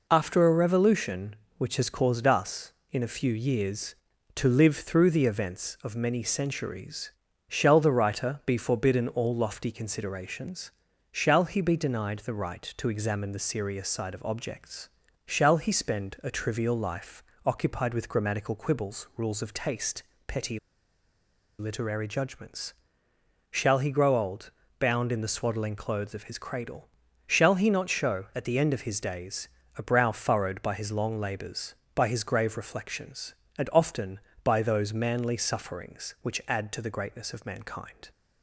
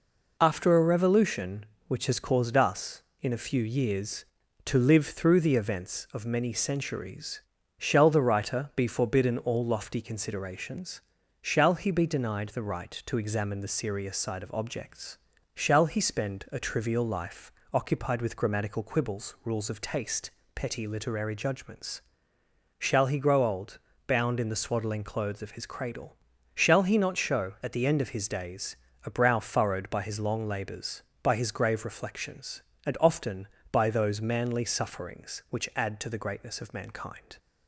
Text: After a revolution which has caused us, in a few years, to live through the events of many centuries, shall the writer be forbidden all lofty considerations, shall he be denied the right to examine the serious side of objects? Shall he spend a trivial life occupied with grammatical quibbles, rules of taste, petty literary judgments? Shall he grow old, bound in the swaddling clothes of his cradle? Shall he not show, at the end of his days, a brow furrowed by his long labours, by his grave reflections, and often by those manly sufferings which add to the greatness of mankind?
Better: second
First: pauses between "life" and "occupied"; slight; at 17.2 s; 0.24 s long // pauses between "petty" and "literary"; at 20.5 s; 1.0 s long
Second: pauses between "life" and "occupied"; slight; at 17.4 s; 0.22 s long

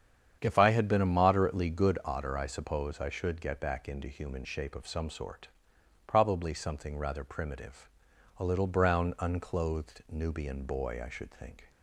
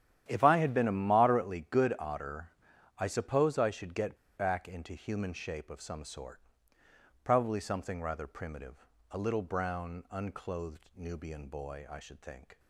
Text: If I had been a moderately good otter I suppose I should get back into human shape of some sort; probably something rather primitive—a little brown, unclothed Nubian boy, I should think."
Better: first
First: starts louder than the rest; strong; until 1.4 s; 8 dB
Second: starts louder than the rest; strong; until 1.2 s; 10.5 dB // pauses between "otter" and "I"; noticeable; at 2.4 s; 0.48 s long // pauses between "get" and "back"; slight; at 4.1 s; 0.19 s long

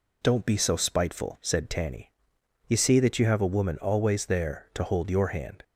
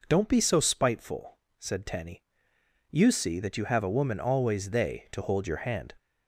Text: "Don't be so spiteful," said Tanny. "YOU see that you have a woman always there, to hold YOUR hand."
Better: first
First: none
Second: says "they" for "there"; at 4.6 s

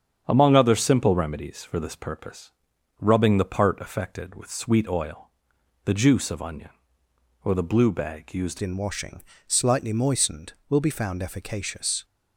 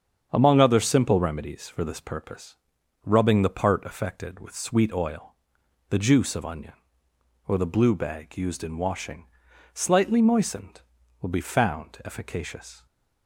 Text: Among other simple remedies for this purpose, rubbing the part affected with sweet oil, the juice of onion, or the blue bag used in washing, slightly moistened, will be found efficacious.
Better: second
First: starts louder than the rest; strong; until 1.2 s; 8 dB // changes voice at "in"; from 8.6 s on; 3.4 s long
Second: starts louder than the rest; strong; until 1.3 s; 7.5 dB

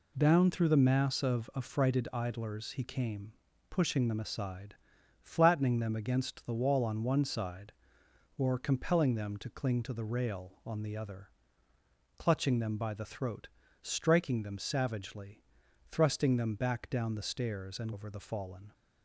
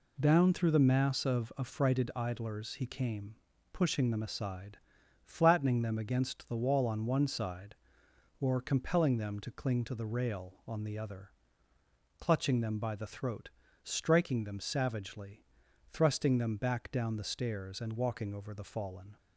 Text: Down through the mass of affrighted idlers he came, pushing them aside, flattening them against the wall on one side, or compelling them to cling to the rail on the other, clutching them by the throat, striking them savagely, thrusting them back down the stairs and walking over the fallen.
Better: second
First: skips "walking"; at 17.9 s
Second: none

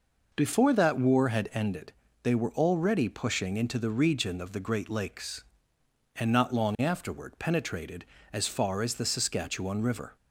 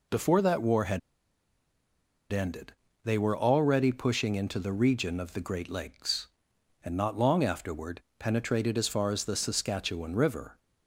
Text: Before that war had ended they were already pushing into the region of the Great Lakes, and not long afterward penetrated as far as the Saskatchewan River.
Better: first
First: pauses between "ended" and "they"; slight; at 1.9 s; 0.32 s long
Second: pauses between "had" and "ended"; strong; at 0.9 s; 1.3 s long // pauses between "ended" and "they"; slight; at 2.7 s; 0.32 s long // pauses between "afterward" and "penetrated"; slight; at 8.0 s; 0.18 s long

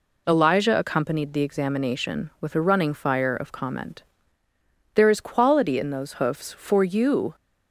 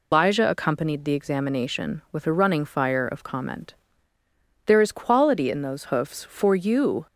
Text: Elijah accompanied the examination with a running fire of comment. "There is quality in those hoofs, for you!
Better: first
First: none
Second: loses the start of "Elijah"; at 0.1 s; 135 ms

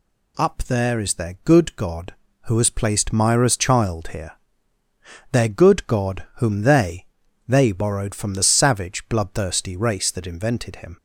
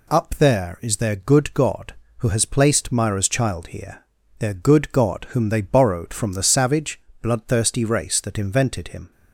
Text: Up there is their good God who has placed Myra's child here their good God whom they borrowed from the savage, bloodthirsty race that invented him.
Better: second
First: pauses between "here" and "their"; at 4.3 s; 1.0 s long // says "they" twice; at 7.4 s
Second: pauses between "here" and "their"; slight; at 4.0 s; 0.36 s long

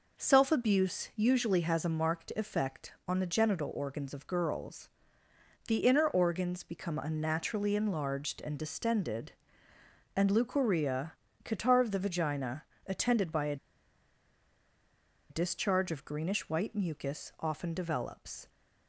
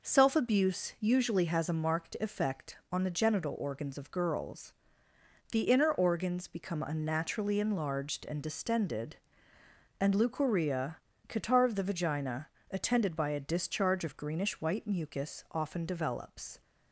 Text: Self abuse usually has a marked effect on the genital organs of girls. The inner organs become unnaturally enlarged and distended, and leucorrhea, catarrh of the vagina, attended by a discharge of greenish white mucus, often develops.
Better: second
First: pauses between "a" and "discharge"; strong; at 13.5 s; 1.7 s long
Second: none

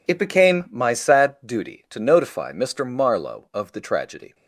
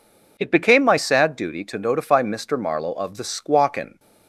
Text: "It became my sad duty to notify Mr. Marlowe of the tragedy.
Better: first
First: none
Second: says "squawkin" for "tragedy"; at 3.2 s

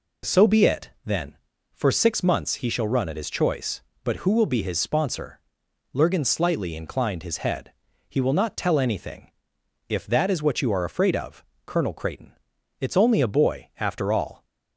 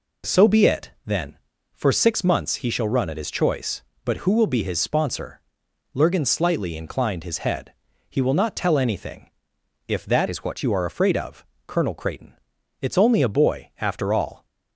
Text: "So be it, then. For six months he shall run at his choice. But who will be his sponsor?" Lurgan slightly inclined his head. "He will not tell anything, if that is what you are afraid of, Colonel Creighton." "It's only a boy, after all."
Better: first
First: none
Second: changes voice from "is" to "what"; from 10.2 to 10.6 s; 0.4 s long

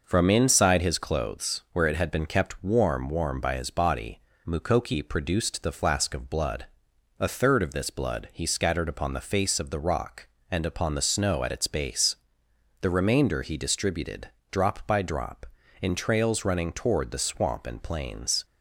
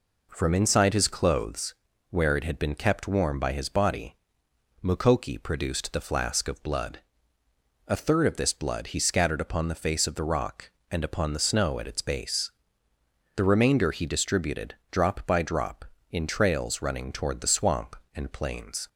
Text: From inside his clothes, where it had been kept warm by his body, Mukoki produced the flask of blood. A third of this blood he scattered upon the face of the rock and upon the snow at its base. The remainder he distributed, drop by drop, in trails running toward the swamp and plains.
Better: second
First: says "warm" twice; at 3.0 s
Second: none

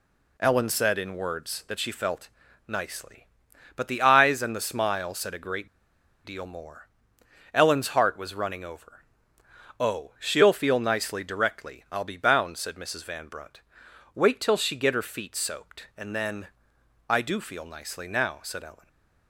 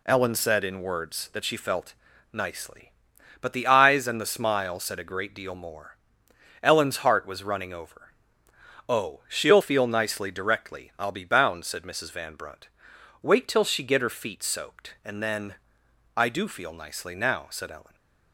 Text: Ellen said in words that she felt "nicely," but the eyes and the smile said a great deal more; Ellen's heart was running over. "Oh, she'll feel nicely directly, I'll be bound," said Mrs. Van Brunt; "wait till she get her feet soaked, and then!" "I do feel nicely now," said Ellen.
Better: second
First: pauses between "felt" and "nicely"; at 2.2 s; 0.40 s long // pauses between "great" and "deal"; noticeable; at 5.6 s; 0.57 s long // stays silent after the last word; slight; from 18.7 s on; 0.5 s long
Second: pauses between "felt" and "nicely"; at 1.9 s; 0.40 s long

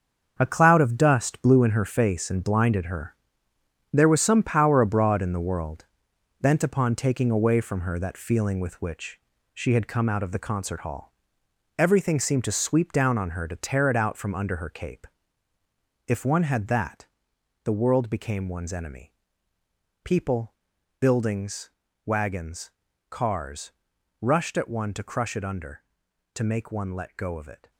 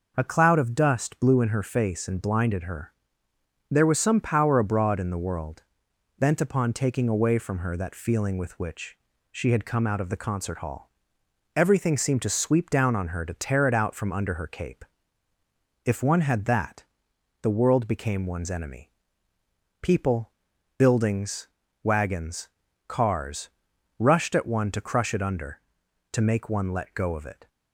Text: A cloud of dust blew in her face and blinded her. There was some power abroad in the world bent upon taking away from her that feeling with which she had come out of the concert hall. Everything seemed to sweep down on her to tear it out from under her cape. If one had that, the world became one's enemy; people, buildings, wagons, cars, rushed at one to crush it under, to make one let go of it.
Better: second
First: gets quieter; strong; throughout; 10 dB // pauses between "world" and "bent"; noticeable; at 5.8 s; 0.54 s long // pauses between "which" and "she"; slight; at 9.1 s; 0.36 s long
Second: pauses between "world" and "bent"; noticeable; at 5.6 s; 0.54 s long // pauses between "which" and "she"; slight; at 8.9 s; 0.36 s long

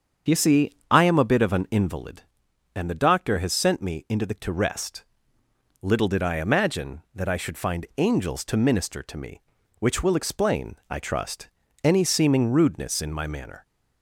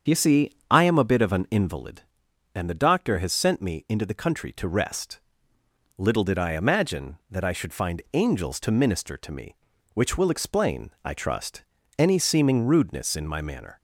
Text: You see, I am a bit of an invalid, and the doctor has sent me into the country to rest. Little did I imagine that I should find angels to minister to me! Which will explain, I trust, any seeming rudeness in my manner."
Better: second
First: starts louder than the rest; strong; until 1.4 s; 7 dB // skips "country"; at 4.3 s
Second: starts louder than the rest; strong; until 1.2 s; 7.5 dB

